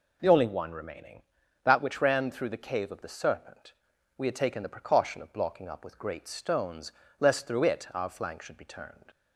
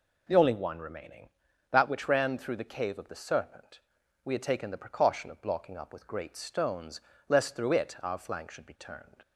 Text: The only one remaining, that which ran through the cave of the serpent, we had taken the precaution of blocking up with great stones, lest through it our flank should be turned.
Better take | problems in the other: neither | none

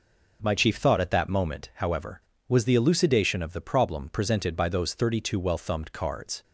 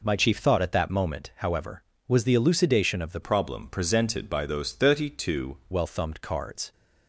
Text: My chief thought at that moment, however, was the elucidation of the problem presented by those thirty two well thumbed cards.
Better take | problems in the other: first | changes voice from "problem" to "two"; from 3.2 to 5.5 s; 2.3 s long

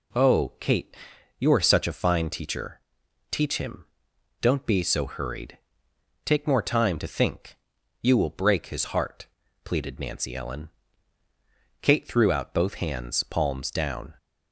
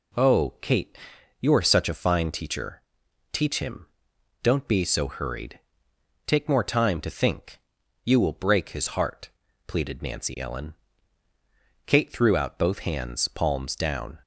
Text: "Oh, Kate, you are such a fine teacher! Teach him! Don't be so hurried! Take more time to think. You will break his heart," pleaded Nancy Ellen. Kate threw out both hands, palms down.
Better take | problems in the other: neither | none

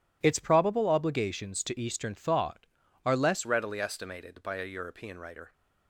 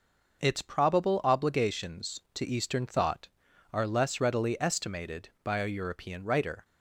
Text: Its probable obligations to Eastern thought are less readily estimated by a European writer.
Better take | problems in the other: second | changes voice at "readily"; from 3.4 s on; 2.1 s long

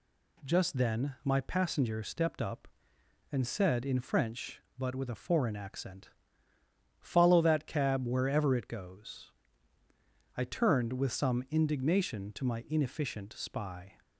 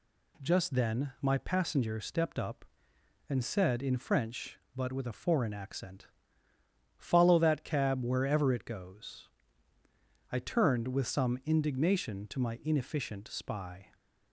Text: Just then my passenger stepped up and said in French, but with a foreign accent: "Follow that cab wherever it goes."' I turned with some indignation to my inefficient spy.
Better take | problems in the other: neither | none

